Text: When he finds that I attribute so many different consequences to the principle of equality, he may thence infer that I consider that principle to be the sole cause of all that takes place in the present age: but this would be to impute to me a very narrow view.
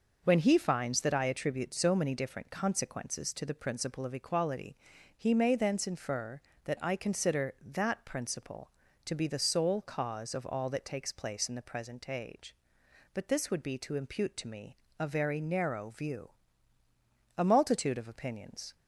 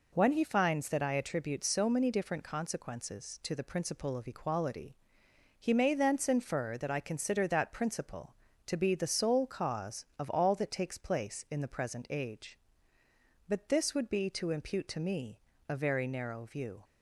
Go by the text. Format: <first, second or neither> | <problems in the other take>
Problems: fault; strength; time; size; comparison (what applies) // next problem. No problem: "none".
second | pauses between "me" and "a"; slight; at 14.7 s; 0.20 s long; slight in the second // goes on to say "A multitude of opinions"; from 17.3 s on; 1.3 s long